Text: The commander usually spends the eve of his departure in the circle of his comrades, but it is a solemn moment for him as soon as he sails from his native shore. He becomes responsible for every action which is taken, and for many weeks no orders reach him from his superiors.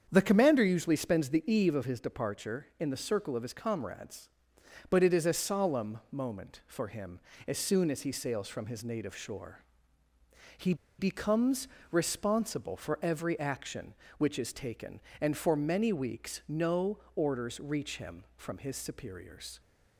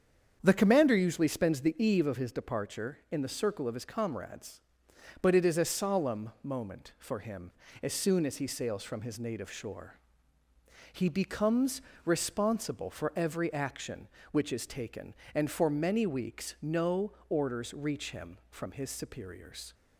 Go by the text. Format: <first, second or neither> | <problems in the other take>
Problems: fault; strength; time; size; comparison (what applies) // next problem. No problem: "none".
second | starts louder than the rest; strong; until 1.1 s; 7.5 dB; strong in the second // pauses between "He" and "becomes"; slight; at 10.7 s; 0.24 s long // pauses between "becomes" and "responsible"; slight; at 11.6 s; 0.26 s long; slight in the second // pauses between "no" and "orders"; slight; at 16.9 s; 0.18 s long; slight in the second